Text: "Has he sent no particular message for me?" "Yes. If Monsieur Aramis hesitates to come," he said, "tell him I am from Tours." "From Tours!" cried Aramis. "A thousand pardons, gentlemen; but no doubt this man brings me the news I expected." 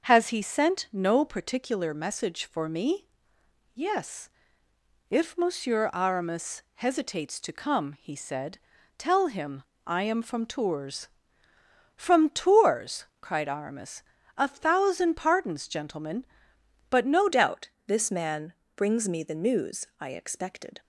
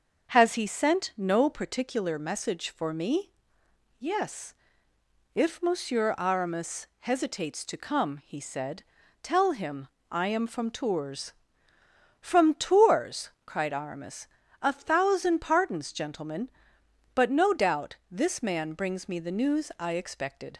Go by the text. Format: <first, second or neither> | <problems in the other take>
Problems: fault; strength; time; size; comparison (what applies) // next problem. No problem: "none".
second | starts louder than the rest; noticeable; until 1.0 s; 6 dB; also in the second // pauses between "him" and "I"; slight; at 9.6 s; 0.24 s long; slight in the second // changes voice at "doubt"; from 17.3 s on; 3.4 s long // pauses between "doubt" and "this"; slight; at 17.6 s; 0.20 s long // pauses between "man" and "brings"; slight; at 18.5 s; 0.24 s long